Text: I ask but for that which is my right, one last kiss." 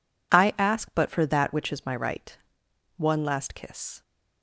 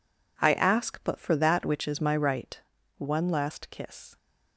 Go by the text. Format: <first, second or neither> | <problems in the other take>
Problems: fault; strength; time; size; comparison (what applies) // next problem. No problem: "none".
neither | none